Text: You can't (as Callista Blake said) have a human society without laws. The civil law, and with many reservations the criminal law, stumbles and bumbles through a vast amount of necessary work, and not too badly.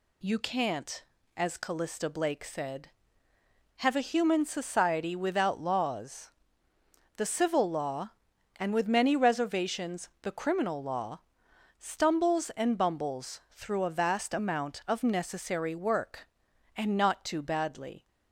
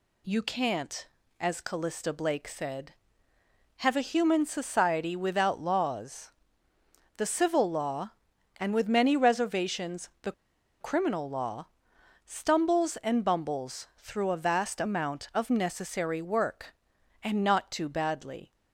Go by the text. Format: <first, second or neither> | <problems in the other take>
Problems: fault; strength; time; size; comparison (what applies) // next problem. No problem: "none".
first | pauses between "the" and "criminal"; noticeable; at 10.3 s; 0.49 s long